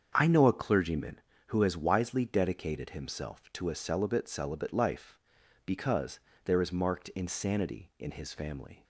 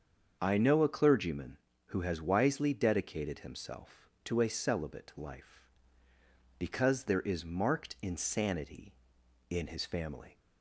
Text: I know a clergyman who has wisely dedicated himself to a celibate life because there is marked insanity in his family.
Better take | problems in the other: second | starts louder than the rest; strong; until 1.1 s; 7.5 dB; also in the second // says "celibate" twice; at 4.2 s // pauses between "because" and "there"; slight; at 6.1 s; 0.24 s long

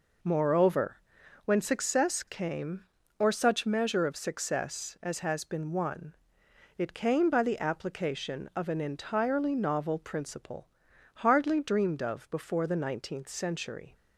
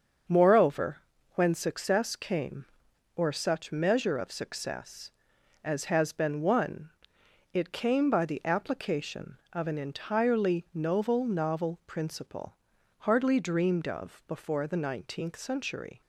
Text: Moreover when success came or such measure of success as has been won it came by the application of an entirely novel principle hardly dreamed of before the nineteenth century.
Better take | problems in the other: first | starts louder than the rest; until 1.6 s; 7 dB // pauses between "Moreover" and "when"; at 0.9 s; 0.38 s long; noticeable in the first // pauses between "won" and "it"; noticeable; at 6.8 s; 0.64 s long; noticeable in the first // says "novel" twice; at 11.2 s // pauses between "principle" and "hardly"; at 12.5 s; 0.42 s long; noticeable in the first

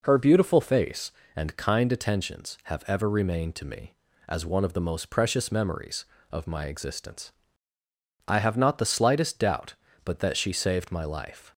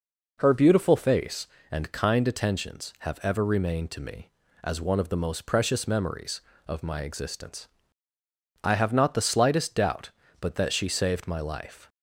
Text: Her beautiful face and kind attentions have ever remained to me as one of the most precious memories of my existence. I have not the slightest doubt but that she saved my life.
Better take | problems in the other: neither | none

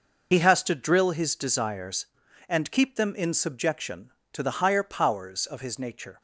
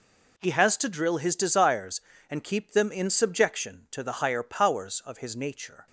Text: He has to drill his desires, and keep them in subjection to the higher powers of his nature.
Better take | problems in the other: second | loses the start of "He"; at 0.3 s; 50 ms

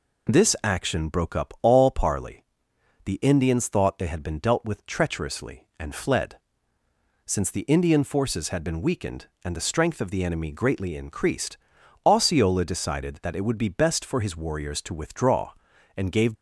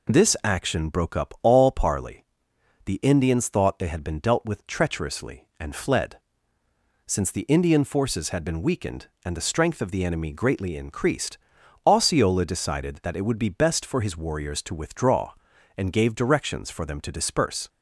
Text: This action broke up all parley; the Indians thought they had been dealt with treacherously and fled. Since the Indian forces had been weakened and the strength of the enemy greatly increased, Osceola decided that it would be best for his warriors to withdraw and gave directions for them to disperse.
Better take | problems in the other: second | stops before "directions for them to disperse"; at 16.3 s

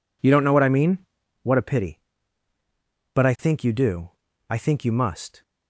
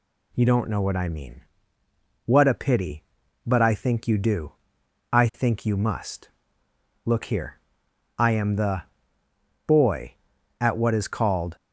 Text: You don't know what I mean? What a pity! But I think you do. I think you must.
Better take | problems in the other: first | goes on to say "Look here I am the Boy at what is called"; strong; from 7.0 s on; 4.5 s long

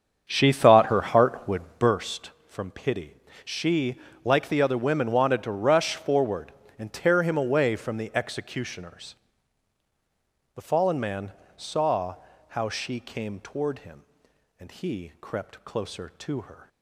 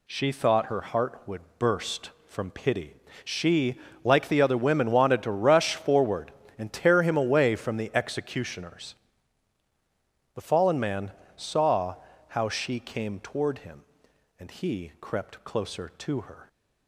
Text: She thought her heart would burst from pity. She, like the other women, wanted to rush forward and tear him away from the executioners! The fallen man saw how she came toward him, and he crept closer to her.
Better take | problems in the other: second | starts louder than the rest; strong; until 2.1 s; 7.5 dB // pauses between "would" and "burst"; slight; at 1.6 s; 0.16 s long; slight in the second // pauses between "man" and "saw"; slight; at 11.3 s; 0.24 s long; slight in the second // pauses between "saw" and "how"; slight; at 12.1 s; 0.32 s long; slight in the second

